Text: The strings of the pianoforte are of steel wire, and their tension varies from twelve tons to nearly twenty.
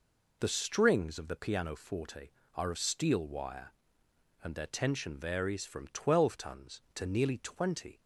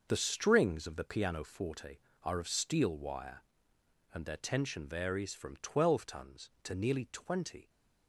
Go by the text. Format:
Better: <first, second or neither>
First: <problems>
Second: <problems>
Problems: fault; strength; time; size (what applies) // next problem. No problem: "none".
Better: first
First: none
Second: gets quieter; strong; throughout; 9 dB